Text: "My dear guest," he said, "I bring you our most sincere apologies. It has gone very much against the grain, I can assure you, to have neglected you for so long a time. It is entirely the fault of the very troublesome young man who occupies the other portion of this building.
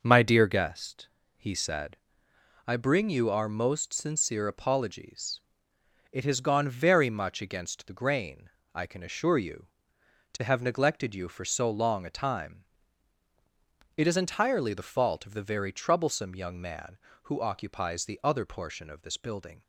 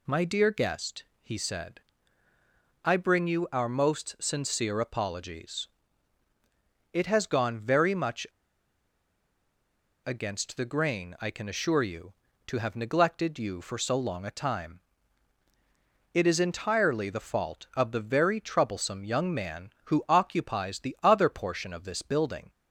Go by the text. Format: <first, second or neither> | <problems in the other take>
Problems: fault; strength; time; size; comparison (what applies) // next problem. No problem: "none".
first | pauses between "much" and "against"; strong; at 8.2 s; 1.7 s long